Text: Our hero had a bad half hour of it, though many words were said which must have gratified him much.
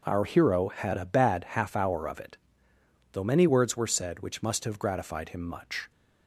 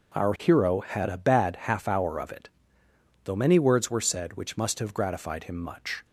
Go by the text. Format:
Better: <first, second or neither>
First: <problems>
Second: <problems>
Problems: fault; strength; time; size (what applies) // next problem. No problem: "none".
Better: neither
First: none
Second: none